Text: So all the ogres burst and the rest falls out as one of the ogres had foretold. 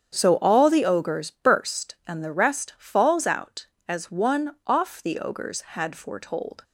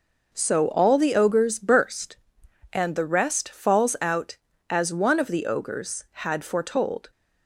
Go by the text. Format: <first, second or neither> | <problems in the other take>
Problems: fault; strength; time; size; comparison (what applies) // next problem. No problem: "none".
second | starts louder than the rest; strong; until 1.2 s; 8 dB // says "off" for "of"; at 4.6 s